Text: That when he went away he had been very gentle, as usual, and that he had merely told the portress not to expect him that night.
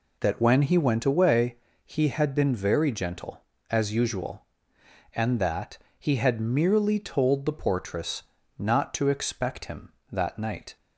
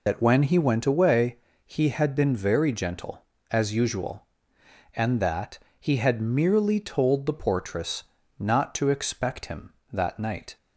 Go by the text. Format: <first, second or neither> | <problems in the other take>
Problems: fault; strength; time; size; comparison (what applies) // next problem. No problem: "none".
first | loses the start of "That"; at 0.0 s; 60 ms // pauses between "away" and "he"; slight; at 1.3 s; 0.28 s long; slight in the first // pauses between "that" and "he"; slight; at 5.5 s; 0.20 s long; slight in the first // pauses between "portress" and "not"; slight; at 8.0 s; 0.34 s long; slight in the first